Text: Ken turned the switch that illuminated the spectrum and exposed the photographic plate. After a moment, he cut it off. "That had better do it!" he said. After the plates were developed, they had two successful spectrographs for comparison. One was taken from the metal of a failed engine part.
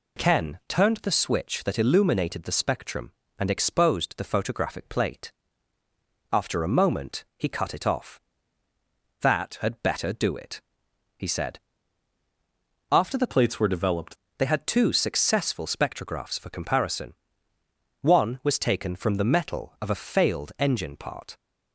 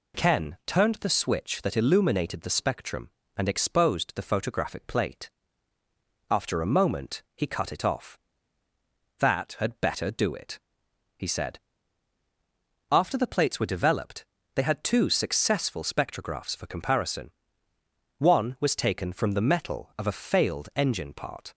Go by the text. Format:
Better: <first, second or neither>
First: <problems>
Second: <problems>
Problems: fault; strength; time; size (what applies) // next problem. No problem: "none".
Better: second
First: changes voice from "plates" to "developed"; from 13.2 to 14.1 s; 0.9 s long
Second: none